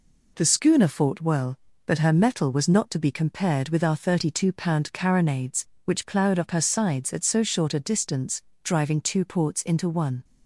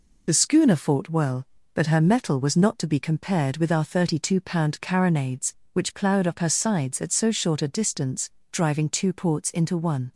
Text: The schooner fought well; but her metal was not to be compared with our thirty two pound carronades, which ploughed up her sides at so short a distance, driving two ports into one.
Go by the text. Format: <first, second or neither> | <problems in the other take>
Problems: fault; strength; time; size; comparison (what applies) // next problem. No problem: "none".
first | loses the start of "The"; at 0.2 s; 40 ms